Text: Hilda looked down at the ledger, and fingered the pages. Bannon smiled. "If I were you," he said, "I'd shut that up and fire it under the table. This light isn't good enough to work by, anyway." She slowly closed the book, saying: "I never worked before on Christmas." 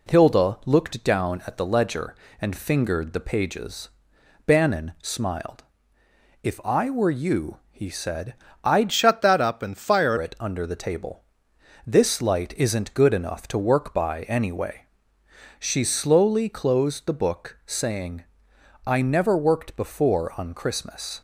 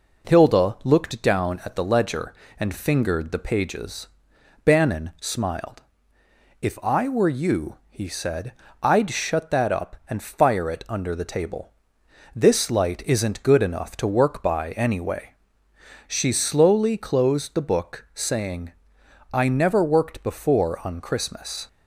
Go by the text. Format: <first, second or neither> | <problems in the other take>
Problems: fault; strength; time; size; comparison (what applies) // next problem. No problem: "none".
second | changes voice from "shut" to "fire"; from 8.9 to 10.1 s; 1.2 s long